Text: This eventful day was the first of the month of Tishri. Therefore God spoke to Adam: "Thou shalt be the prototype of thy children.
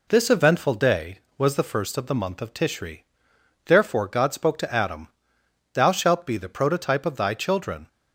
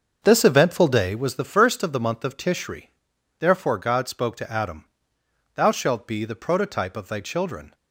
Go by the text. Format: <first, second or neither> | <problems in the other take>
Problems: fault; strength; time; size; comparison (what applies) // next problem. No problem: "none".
first | starts louder than the rest; until 1.4 s; 6.5 dB